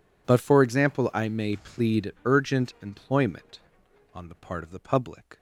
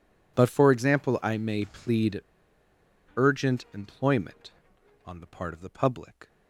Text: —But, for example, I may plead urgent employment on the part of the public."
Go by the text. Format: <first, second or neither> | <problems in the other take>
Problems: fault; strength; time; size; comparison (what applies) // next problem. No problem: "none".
first | pauses between "plead" and "urgent"; noticeable; at 2.2 s; 0.94 s long